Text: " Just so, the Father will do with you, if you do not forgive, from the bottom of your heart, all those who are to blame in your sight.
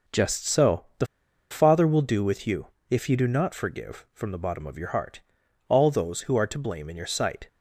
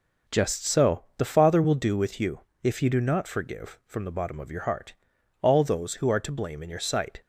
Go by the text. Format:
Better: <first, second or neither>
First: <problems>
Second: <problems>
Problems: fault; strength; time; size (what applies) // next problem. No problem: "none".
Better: second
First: pauses between "the" and "Father"; at 1.0 s; 0.45 s long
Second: none